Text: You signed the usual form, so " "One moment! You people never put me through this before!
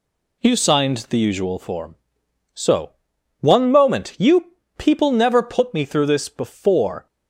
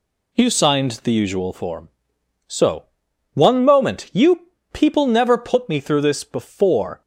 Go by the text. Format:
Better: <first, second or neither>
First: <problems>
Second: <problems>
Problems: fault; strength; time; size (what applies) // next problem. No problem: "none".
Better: neither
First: pauses between "You" and "people"; slight; at 4.4 s; 0.32 s long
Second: pauses between "You" and "people"; slight; at 4.4 s; 0.32 s long